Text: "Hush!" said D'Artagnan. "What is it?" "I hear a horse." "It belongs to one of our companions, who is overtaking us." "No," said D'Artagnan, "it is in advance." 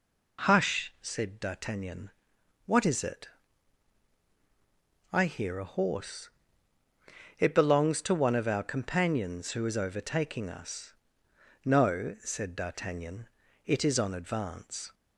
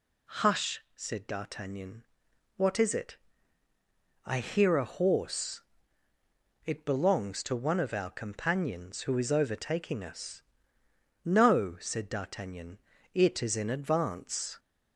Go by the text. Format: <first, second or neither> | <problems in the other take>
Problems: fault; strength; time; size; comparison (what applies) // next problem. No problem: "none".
second | says "on" for "in"; at 13.9 s